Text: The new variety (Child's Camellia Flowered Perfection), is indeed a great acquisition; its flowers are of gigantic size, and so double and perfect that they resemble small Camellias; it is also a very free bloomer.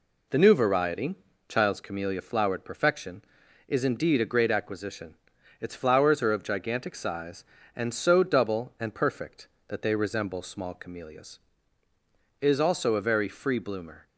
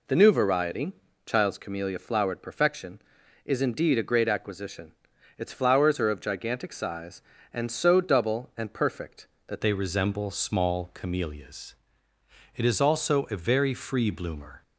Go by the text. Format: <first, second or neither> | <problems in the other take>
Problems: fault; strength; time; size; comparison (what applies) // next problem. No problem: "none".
first | changes voice at "they"; from 9.6 s on; 5.0 s long